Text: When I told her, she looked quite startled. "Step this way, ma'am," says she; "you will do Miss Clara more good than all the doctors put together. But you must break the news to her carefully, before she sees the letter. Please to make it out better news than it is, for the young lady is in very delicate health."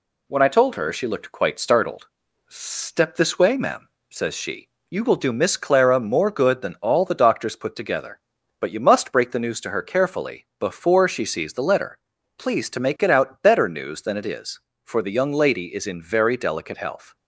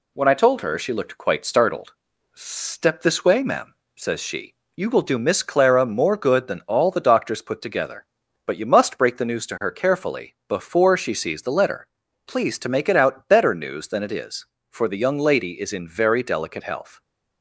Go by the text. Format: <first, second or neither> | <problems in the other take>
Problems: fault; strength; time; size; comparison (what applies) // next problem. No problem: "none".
neither | none